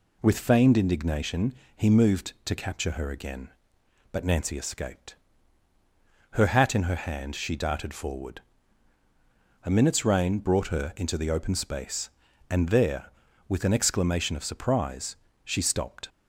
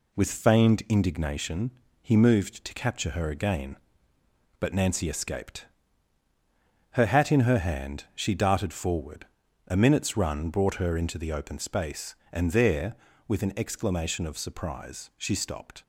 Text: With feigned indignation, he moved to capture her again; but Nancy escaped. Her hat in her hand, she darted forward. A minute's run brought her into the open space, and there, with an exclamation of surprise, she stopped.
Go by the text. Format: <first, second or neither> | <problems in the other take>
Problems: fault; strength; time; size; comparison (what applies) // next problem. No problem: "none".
second | says "rain" for "run"; at 10.0 s